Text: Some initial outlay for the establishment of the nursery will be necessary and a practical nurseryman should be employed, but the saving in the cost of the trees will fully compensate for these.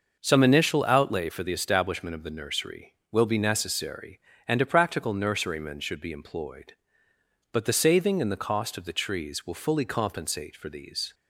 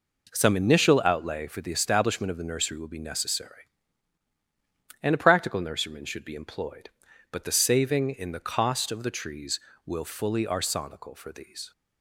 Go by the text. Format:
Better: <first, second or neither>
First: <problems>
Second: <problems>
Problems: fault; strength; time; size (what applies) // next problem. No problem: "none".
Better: first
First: none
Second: says "arsonical" for "compensate"; at 10.4 s